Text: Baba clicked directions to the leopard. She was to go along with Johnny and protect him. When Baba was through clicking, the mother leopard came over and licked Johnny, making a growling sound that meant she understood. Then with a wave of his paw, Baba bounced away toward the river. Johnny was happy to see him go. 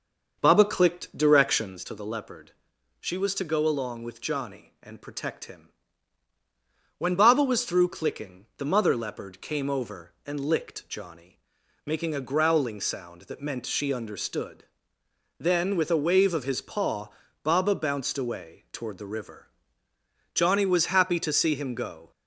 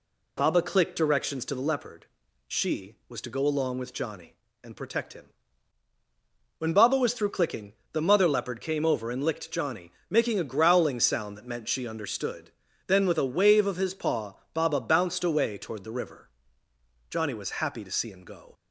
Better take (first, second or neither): second